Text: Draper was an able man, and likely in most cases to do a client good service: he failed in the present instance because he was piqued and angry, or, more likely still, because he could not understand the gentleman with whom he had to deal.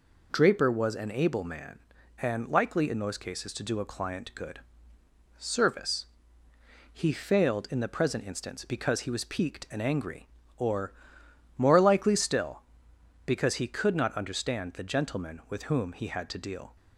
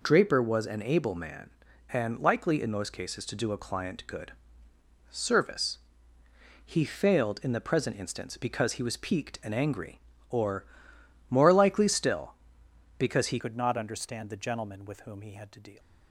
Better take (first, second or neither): first